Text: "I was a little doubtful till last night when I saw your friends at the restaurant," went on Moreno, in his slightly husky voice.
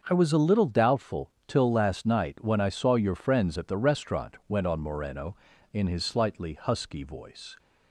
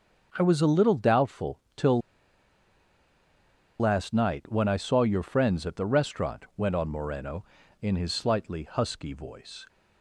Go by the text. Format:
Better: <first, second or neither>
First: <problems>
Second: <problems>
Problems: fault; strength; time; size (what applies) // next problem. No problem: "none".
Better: first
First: starts louder than the rest; until 1.0 s; 6 dB // pauses between "doubtful" and "till"; slight; at 1.2 s; 0.16 s long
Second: starts louder than the rest; until 1.3 s; 6 dB // pauses between "doubtful" and "till"; slight; at 1.5 s; 0.16 s long // pauses between "till" and "last"; strong; at 2.0 s; 1.8 s long